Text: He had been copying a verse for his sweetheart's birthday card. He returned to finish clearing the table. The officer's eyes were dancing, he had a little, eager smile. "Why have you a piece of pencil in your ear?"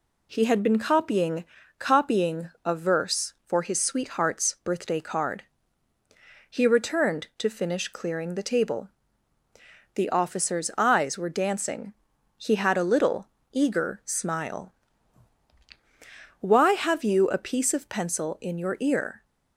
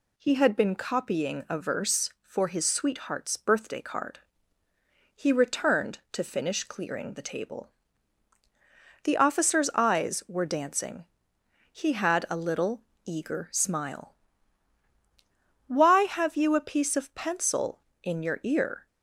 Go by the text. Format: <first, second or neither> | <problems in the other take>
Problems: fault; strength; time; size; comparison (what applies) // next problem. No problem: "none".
second | says "copying" twice; at 1.8 s